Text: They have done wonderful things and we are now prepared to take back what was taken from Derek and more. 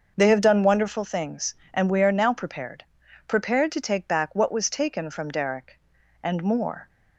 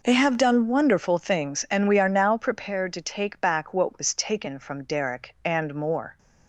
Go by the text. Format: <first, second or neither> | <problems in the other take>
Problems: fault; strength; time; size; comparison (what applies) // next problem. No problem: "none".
second | starts louder than the rest; until 1.1 s; 6 dB // says "prepared" twice; at 3.2 s